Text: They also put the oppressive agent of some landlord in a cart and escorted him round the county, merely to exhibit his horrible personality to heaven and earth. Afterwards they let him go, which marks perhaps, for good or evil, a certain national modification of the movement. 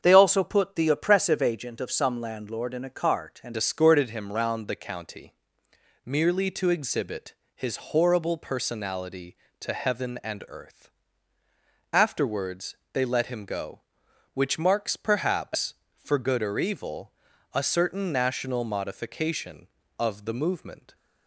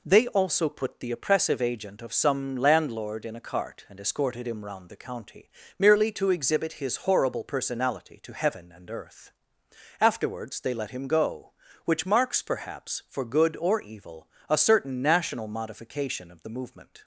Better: second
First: starts louder than the rest; until 1.0 s; 7 dB // changes voice at "escorted"; from 3.5 s on; 17.4 s long // pauses between "exhibit" and "his"; slight; at 7.3 s; 0.20 s long // pauses between "Afterwards" and "they"; slight; at 12.7 s; 0.18 s long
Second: none

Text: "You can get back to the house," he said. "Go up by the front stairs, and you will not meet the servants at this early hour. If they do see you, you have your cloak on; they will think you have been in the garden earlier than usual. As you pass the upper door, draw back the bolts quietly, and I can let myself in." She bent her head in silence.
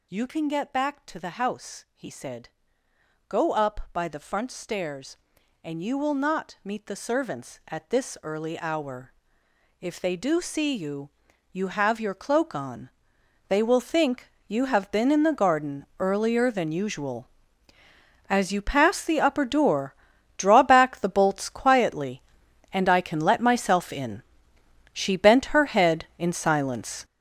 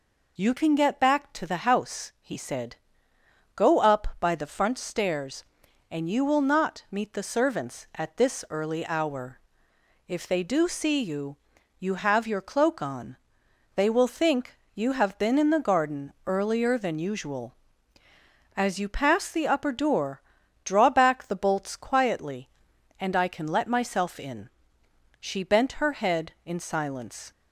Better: second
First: gets louder; strong; throughout; 9.5 dB // pauses between "think" and "you"; slight; at 14.3 s; 0.16 s long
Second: pauses between "think" and "you"; slight; at 14.5 s; 0.16 s long

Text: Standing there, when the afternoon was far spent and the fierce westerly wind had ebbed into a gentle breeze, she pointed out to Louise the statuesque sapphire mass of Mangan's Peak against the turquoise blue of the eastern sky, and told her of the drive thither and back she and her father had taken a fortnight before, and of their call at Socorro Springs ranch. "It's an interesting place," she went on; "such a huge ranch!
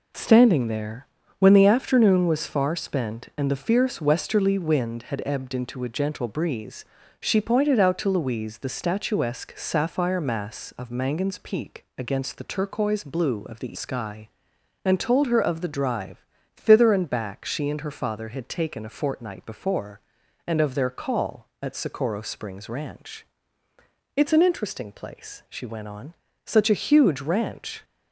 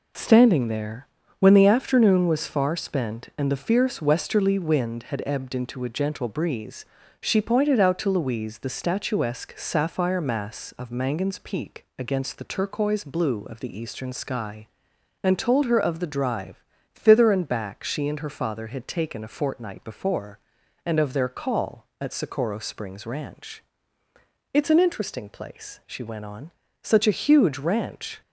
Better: second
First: skips "eastern"; at 13.7 s // pauses between "drive" and "thither"; slight; at 16.2 s; 0.32 s long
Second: pauses between "drive" and "thither"; slight; at 16.6 s; 0.32 s long

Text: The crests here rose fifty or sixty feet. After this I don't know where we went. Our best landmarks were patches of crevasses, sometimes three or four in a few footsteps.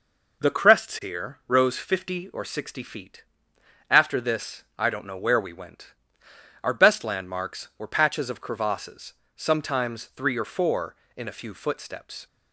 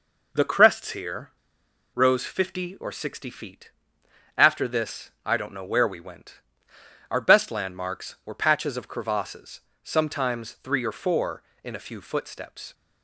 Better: first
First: pauses between "this" and "I"; slight; at 4.6 s; 0.16 s long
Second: pauses between "here" and "rose"; noticeable; at 1.2 s; 0.67 s long // pauses between "this" and "I"; slight; at 5.0 s; 0.16 s long

